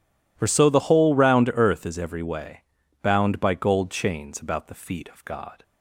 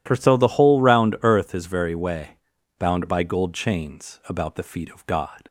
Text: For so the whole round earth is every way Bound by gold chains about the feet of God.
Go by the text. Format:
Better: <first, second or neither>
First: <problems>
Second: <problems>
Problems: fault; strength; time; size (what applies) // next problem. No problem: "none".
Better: first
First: pauses between "way" and "Bound"; at 2.6 s; 0.38 s long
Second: says "very" for "every"; at 1.6 s // pauses between "way" and "Bound"; at 2.3 s; 0.42 s long